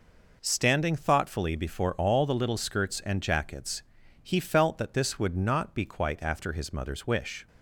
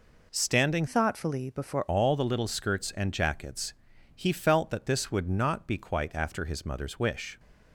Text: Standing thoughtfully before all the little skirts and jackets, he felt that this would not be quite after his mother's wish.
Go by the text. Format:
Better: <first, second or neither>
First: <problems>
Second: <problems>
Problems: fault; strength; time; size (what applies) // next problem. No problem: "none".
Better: first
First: none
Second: changes voice from "thoughtfully" to "before"; from 0.8 to 1.8 s; 1.0 s long